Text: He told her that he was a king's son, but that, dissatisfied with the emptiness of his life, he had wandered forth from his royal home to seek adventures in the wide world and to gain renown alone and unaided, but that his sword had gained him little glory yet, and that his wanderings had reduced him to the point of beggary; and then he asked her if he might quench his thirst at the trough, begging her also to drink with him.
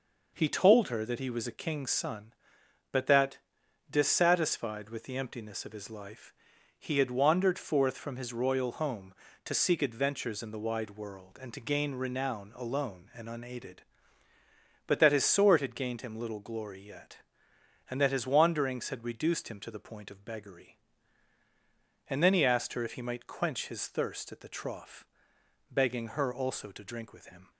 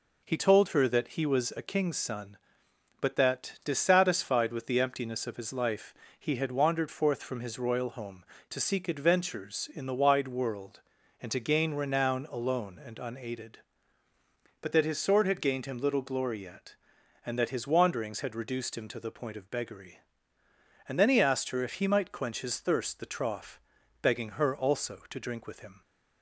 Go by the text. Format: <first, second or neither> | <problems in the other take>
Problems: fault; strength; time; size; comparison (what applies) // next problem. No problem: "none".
first | skips "at"; at 23.0 s